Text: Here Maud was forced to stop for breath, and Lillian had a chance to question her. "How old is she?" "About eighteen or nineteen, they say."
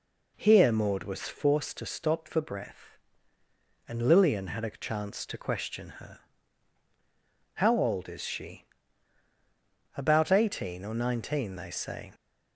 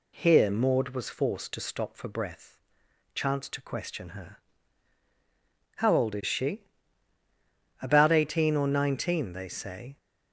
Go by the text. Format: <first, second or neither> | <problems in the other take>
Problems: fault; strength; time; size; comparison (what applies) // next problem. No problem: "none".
first | skips "and Lillian had a"; at 2.8 s